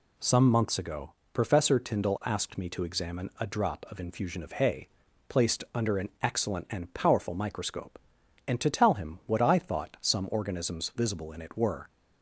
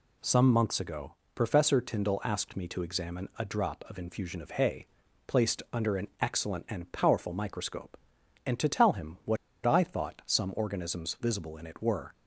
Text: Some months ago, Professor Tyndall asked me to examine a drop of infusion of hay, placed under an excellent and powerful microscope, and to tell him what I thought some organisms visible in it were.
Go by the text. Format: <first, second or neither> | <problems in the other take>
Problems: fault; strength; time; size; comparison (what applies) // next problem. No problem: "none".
first | pauses between "what" and "I"; slight; at 9.3 s; 0.28 s long